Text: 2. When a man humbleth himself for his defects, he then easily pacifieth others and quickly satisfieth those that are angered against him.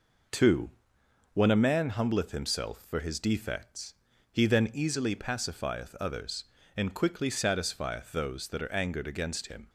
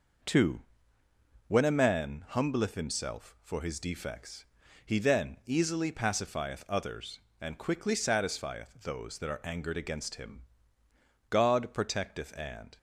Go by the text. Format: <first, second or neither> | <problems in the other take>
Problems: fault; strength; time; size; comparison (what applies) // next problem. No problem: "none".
first | goes on to say "God protecteth and"; from 11.3 s on; 1.4 s long